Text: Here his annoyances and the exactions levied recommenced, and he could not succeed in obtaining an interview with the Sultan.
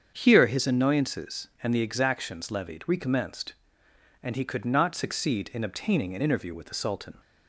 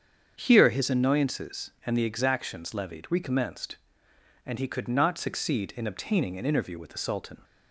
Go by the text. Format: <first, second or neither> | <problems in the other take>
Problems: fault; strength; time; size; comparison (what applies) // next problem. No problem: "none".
neither | starts louder than the rest; strong; the same in both